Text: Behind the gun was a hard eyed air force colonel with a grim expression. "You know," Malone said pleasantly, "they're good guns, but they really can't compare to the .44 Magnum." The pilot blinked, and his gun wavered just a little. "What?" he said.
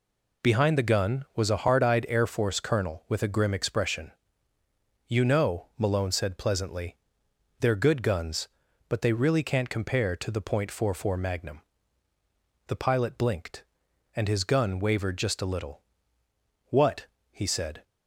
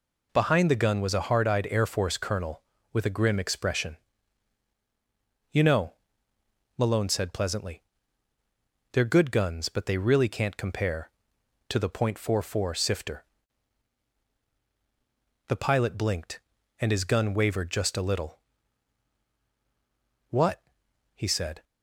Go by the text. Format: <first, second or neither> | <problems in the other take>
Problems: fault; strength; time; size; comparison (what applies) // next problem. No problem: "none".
first | says "Sifter" for "Magnum"; at 12.7 s